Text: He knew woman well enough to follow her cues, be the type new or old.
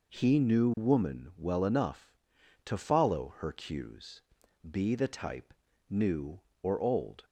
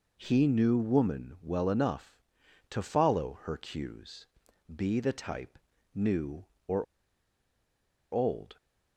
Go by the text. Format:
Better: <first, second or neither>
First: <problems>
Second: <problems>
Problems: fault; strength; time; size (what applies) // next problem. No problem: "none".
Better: first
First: pauses between "type" and "new"; slight; at 5.5 s; 0.34 s long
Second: pauses between "type" and "new"; slight; at 5.5 s; 0.34 s long // pauses between "or" and "old"; strong; at 6.8 s; 1.2 s long